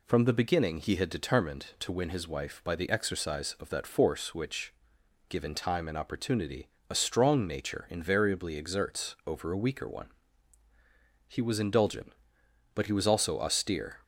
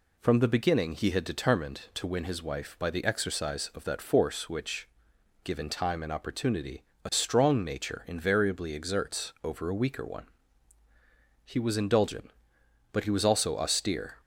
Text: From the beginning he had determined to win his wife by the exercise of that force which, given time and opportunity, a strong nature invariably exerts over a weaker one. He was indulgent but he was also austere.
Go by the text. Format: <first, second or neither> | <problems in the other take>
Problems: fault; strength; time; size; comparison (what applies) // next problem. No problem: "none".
neither | none